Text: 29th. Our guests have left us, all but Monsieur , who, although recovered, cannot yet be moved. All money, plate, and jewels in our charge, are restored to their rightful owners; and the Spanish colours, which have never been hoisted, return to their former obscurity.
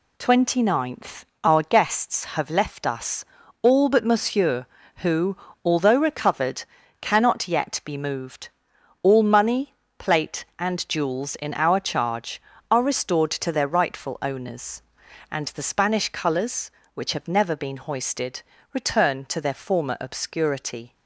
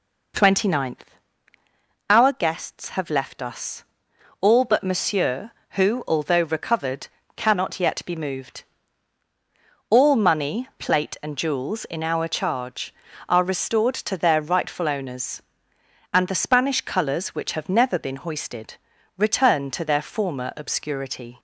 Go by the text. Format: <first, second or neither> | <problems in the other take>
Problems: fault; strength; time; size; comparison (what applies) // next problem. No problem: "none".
neither | none